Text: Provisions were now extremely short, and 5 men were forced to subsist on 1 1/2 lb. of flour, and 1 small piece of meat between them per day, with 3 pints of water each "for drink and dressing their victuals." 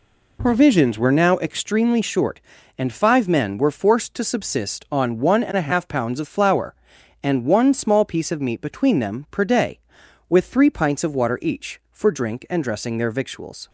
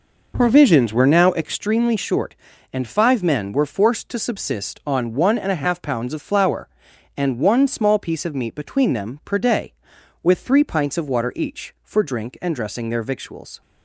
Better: first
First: none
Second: starts louder than the rest; noticeable; until 1.5 s; 5 dB

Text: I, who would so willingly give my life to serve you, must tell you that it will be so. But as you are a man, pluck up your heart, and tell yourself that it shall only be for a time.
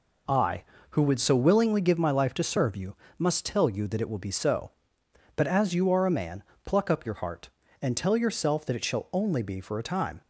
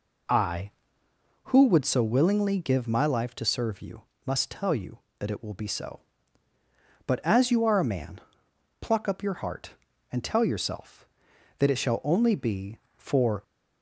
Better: first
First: none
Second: stops before "a time"; at 13.4 s

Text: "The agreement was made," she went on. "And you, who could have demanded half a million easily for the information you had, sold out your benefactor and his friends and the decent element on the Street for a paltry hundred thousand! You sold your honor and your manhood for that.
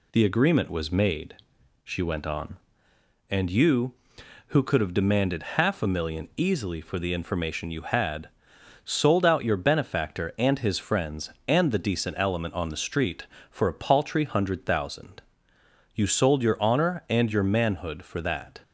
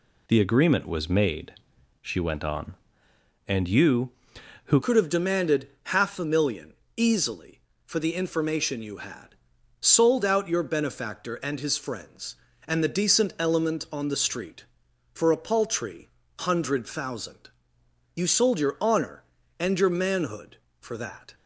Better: first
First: none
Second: changes voice at "could"; from 4.8 s on; 16.5 s long // pauses between "demanded" and "half"; slight; at 5.6 s; 0.16 s long // pauses between "million" and "easily"; slight; at 6.7 s; 0.22 s long // pauses between "paltry" and "hundred"; slight; at 16.0 s; 0.32 s long

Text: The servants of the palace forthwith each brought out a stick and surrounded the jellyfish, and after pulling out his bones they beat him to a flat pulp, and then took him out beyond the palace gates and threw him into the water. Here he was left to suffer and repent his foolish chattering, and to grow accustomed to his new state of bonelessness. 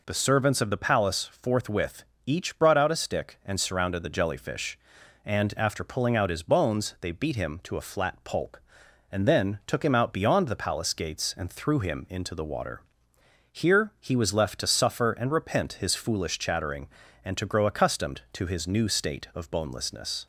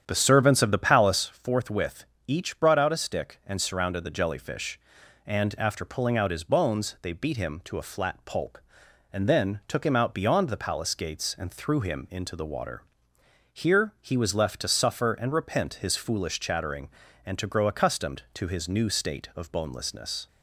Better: first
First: pauses between "forthwith" and "each"; slight; at 2.0 s; 0.24 s long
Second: starts louder than the rest; strong; until 1.4 s; 9 dB // pauses between "forthwith" and "each"; slight; at 2.0 s; 0.24 s long

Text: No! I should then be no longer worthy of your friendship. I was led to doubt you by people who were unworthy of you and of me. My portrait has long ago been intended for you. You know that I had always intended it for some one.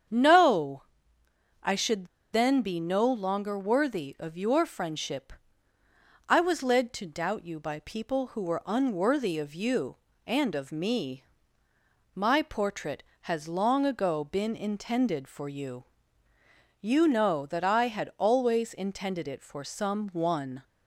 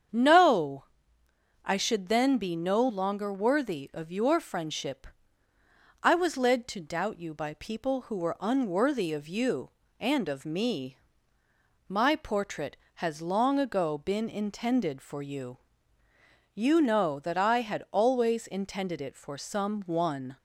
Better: second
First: starts louder than the rest; strong; until 1.8 s; 8 dB // pauses between "should" and "then"; slight; at 2.0 s; 0.27 s long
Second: starts louder than the rest; strong; until 1.8 s; 8 dB

